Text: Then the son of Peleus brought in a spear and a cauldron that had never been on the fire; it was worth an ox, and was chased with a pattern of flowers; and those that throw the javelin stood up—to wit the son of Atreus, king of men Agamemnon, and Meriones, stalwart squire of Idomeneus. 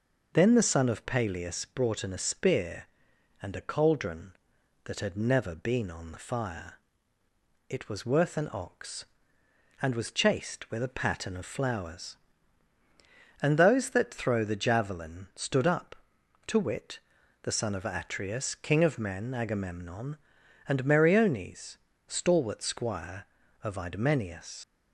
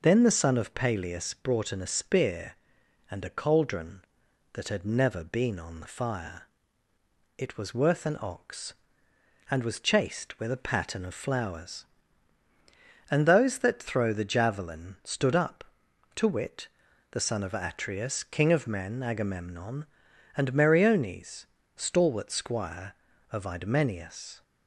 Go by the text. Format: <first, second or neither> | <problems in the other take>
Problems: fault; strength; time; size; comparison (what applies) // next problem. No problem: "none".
second | pauses between "wit" and "the"; at 16.9 s; 0.44 s long; also in the second // leaves "Idomeneus" unfinished; at 24.6 s; 105 ms